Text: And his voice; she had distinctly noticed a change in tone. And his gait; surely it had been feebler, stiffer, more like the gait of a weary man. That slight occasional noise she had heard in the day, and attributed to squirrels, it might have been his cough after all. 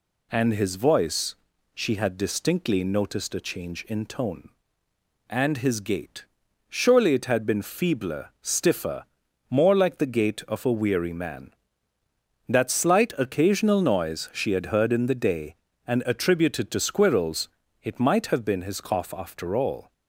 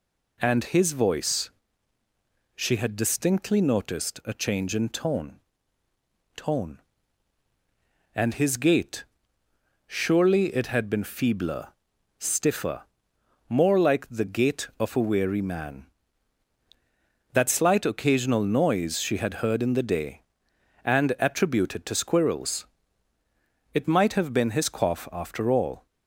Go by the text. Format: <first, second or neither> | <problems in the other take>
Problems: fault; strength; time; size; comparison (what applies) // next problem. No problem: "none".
first | says "tone" twice; at 6.3 s